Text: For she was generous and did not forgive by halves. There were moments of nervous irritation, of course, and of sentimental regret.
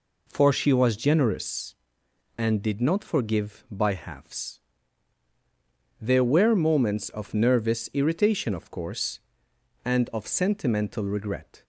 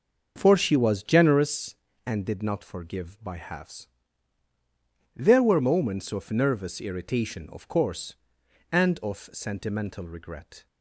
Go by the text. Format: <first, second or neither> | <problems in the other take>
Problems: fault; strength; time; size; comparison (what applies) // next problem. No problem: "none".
first | starts louder than the rest; until 1.4 s; 6.5 dB